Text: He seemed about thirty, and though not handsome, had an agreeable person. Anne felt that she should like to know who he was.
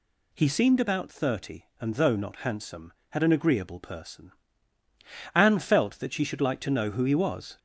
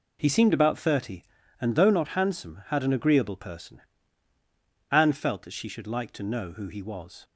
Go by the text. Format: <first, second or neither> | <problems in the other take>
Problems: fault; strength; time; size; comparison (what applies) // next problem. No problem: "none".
second | gets louder; slight; throughout; 3 dB